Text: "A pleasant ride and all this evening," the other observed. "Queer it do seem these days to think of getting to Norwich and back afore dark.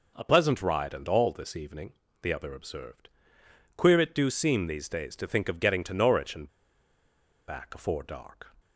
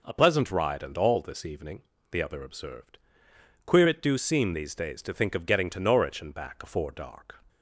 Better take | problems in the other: second | pauses between "and" and "back"; at 6.4 s; 1.0 s long

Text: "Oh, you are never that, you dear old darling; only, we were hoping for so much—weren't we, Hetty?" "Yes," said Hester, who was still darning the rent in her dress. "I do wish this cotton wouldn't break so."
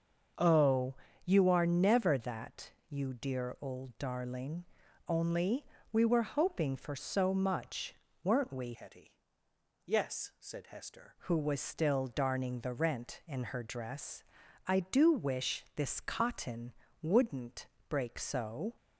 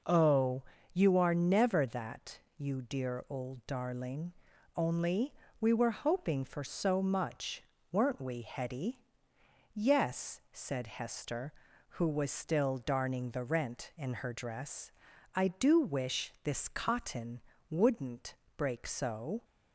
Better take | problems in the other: second | starts louder than the rest; until 1.6 s; 6.5 dB // changes voice from "Hetty" to "Hester"; from 8.7 to 11.1 s; 2.4 s long // pauses between "cotton" and "wouldn't"; slight; at 16.7 s; 0.26 s long; slight in the second // pauses between "wouldn't" and "break"; slight; at 17.6 s; 0.20 s long; slight in the second

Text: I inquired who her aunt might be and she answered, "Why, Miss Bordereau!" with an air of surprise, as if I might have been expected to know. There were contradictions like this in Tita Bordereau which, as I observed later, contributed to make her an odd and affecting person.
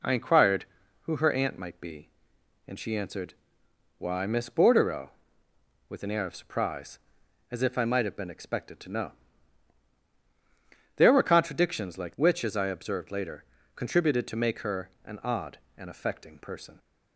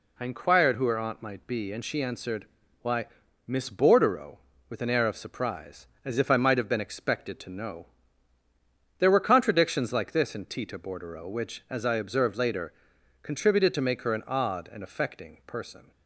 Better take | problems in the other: second | skips "this in Tita Bordereau"; at 12.1 s // pauses between "her" and "an"; slight; at 14.8 s; 0.16 s long

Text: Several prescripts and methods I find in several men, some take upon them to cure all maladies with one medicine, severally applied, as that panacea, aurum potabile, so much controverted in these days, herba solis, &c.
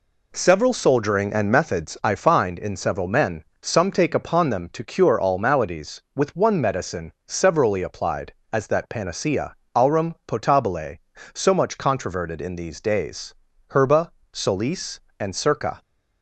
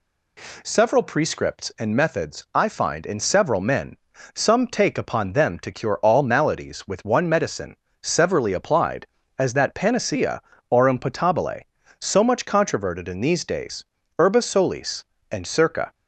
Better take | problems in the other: second | says "soldiering" for "prescripts"; at 0.7 s // pauses between "herba" and "solis"; slight; at 14.1 s; 0.20 s long

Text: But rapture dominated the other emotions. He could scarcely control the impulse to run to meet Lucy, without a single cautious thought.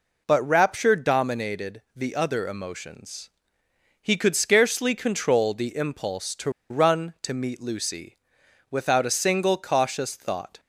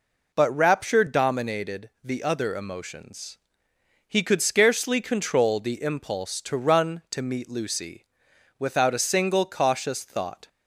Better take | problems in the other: second | pauses between "to" and "run"; slight; at 6.4 s; 0.20 s long

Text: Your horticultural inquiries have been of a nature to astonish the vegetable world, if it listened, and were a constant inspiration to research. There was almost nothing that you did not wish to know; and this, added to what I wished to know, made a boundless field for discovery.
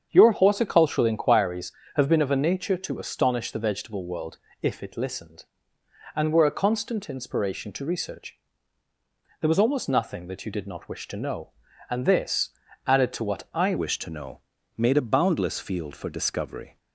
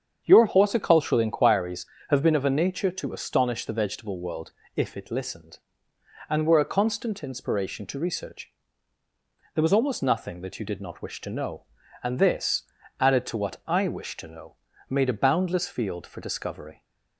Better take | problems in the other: second | starts louder than the rest; strong; until 1.1 s; 7.5 dB; strong in the second // changes voice at "wished"; from 13.7 s on; 3.0 s long

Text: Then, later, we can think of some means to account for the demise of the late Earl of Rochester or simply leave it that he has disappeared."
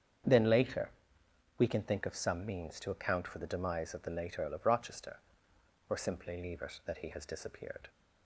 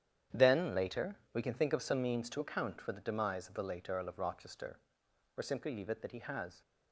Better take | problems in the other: first | starts louder than the rest; strong; until 1.5 s; 9.5 dB; strong in the first // stops before "disappeared"; at 6.6 s

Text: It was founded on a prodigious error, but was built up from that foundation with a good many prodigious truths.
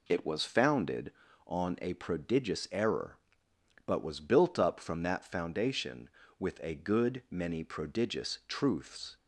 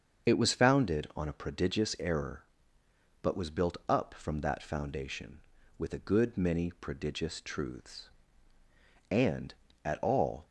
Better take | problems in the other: first | starts louder than the rest; until 1.3 s; 6.5 dB // goes on to say "And at all"; from 9.1 s on; 1.3 s long

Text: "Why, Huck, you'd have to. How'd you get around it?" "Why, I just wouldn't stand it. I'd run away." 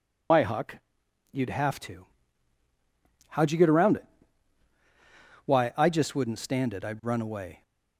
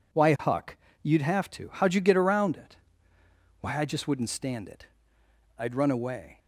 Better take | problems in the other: second | loses the start of "Why"; at 0.3 s; 110 ms

